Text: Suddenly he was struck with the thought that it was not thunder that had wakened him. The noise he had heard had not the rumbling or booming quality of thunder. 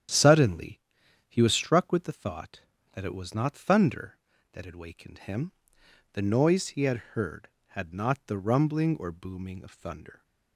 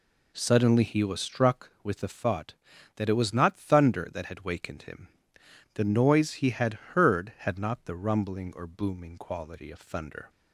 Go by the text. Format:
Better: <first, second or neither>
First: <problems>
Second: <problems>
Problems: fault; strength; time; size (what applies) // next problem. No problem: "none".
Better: second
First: starts louder than the rest; strong; until 1.6 s; 9.5 dB // pauses between "Suddenly" and "he"; noticeable; at 0.7 s; 0.48 s long // pauses between "had" and "heard"; slight; at 6.9 s; 0.16 s long // skips "quality"; at 9.6 s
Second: pauses between "had" and "heard"; slight; at 6.7 s; 0.20 s long